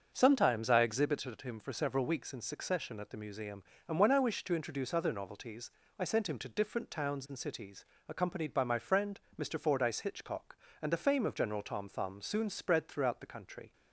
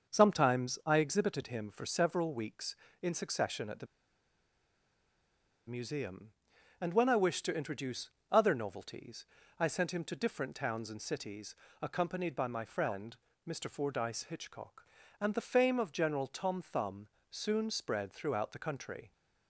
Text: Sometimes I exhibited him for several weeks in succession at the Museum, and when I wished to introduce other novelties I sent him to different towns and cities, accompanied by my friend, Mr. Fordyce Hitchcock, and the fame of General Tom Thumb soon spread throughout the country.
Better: first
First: starts louder than the rest; until 1.1 s; 6.5 dB // pauses between "novelties" and "I"; slight; at 5.7 s; 0.26 s long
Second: starts louder than the rest; until 1.1 s; 6.5 dB // pauses between "the" and "Museum"; strong; at 3.8 s; 1.8 s long // pauses between "introduce" and "other"; slight; at 8.1 s; 0.20 s long // pauses between "novelties" and "I"; slight; at 9.2 s; 0.36 s long // pauses between "Thumb" and "soon"; slight; at 17.0 s; 0.24 s long

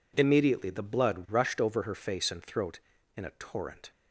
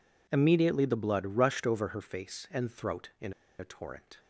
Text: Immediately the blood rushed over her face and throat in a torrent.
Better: first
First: none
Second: pauses between "in" and "a"; slight; at 3.3 s; 0.27 s long

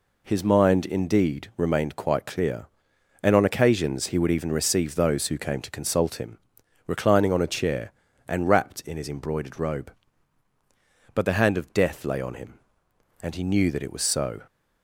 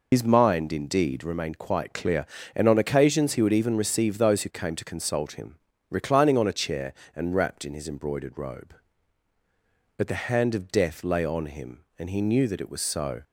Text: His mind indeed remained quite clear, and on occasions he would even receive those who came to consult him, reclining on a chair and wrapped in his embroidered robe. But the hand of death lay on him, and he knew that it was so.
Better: first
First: none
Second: loses the start of "His"; at 0.1 s; 90 ms

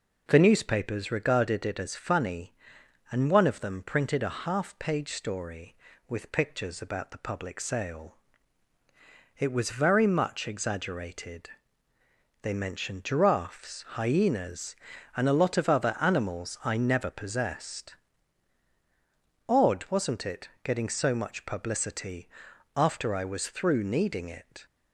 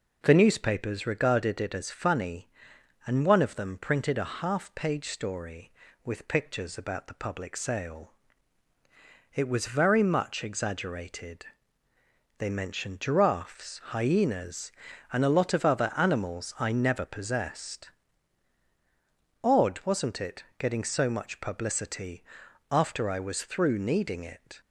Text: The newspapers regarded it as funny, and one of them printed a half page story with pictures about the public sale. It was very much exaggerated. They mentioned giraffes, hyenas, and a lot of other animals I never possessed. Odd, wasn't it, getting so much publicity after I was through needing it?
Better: neither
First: pauses between "publicity" and "after"; noticeable; at 22.2 s; 0.48 s long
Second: pauses between "publicity" and "after"; noticeable; at 22.2 s; 0.48 s long

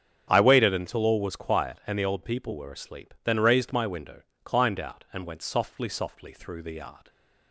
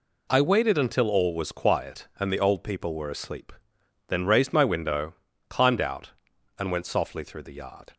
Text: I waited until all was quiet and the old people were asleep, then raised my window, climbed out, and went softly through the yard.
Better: second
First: starts louder than the rest; strong; until 1.3 s; 8 dB // says "softly" twice; at 5.8 s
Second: none

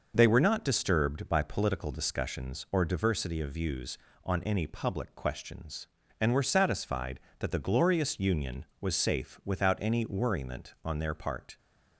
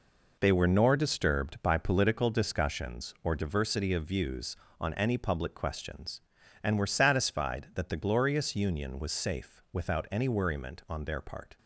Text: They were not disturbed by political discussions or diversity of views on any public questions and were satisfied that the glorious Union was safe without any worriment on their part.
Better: first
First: none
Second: says "nor" for "not"; at 0.6 s

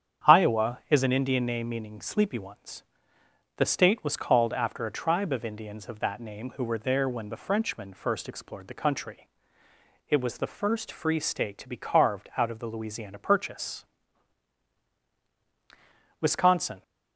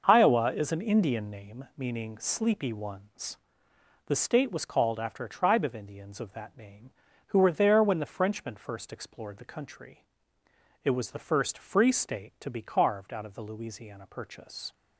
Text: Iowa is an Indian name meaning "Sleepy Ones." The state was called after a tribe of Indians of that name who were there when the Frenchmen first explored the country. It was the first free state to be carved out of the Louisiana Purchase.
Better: second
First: starts louder than the rest; strong; until 1.3 s; 8.5 dB // goes on to say "Wisconsin"; noticeable; from 16.2 s on; 0.62 s long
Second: starts louder than the rest; noticeable; until 1.0 s; 6 dB

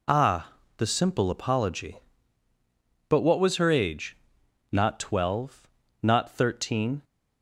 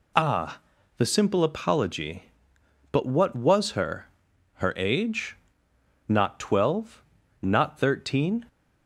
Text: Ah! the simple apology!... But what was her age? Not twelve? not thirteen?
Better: first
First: none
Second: says "her" twice; at 4.5 s

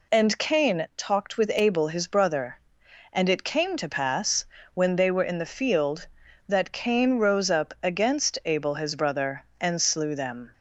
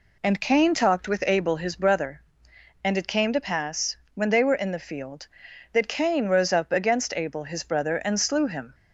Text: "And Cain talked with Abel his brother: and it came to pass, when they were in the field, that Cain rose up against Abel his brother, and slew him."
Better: second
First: says "them" for "him"; at 10.1 s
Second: none

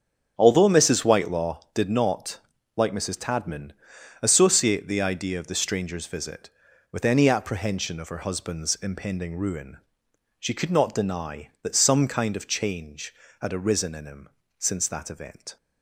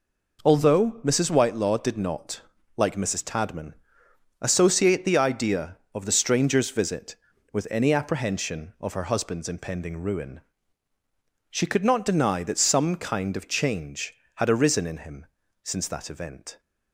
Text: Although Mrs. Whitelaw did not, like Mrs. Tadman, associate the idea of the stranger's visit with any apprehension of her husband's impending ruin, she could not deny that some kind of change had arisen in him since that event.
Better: second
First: starts louder than the rest; strong; until 1.7 s; 8 dB // pauses between "him" and "since"; slight; at 14.2 s; 0.30 s long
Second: pauses between "him" and "since"; at 15.2 s; 0.38 s long

